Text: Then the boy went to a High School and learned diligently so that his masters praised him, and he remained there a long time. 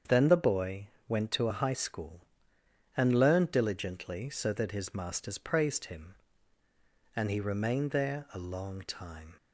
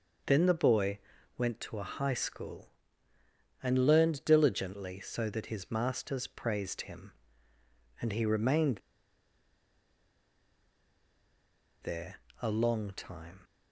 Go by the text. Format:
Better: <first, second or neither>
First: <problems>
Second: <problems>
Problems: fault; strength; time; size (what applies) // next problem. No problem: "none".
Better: first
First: starts louder than the rest; strong; until 1.2 s; 7.5 dB // pauses between "boy" and "went"; slight; at 0.8 s; 0.22 s long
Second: starts louder than the rest; noticeable; until 1.6 s; 6 dB // pauses between "boy" and "went"; at 0.9 s; 0.38 s long // pauses between "remained" and "there"; strong; at 8.7 s; 3.0 s long // pauses between "there" and "a"; slight; at 12.1 s; 0.26 s long